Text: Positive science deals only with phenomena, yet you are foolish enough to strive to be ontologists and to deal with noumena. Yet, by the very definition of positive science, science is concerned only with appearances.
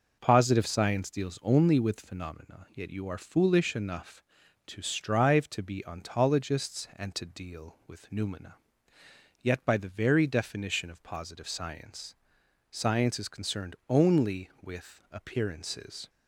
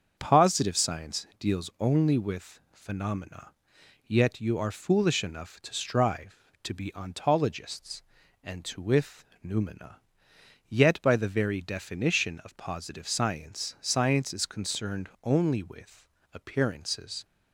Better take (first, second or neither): first